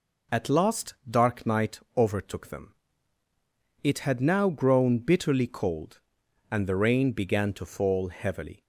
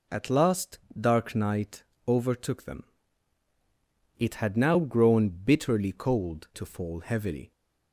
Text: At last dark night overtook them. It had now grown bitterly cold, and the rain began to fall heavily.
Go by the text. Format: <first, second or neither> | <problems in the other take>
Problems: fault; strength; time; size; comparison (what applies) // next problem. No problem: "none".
first | pauses between "last" and "dark"; slight; at 0.7 s; 0.20 s long // pauses between "night" and "overtook"; slight; at 1.8 s; 0.24 s long; slight in the first // skips "and the rain began"; at 6.4 s